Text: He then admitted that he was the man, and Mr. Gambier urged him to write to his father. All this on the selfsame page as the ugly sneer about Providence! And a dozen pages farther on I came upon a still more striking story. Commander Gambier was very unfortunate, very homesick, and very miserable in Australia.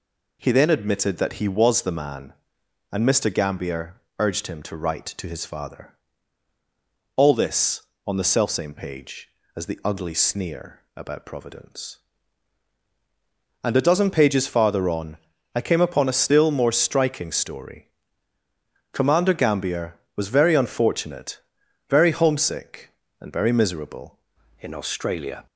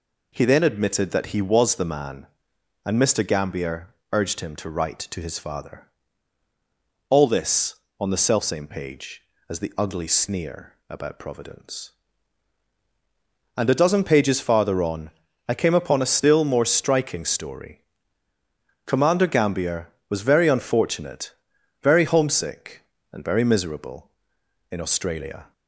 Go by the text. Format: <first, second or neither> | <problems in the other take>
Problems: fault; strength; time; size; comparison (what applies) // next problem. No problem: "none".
second | pauses between "Gambier" and "urged"; slight; at 4.0 s; 0.18 s long; slight in the second // pauses between "sneer" and "about"; slight; at 10.8 s; 0.16 s long; slight in the second // pauses between "on" and "I"; slight; at 15.1 s; 0.36 s long; slight in the second // changes voice at "in"; from 24.5 s on; 0.9 s long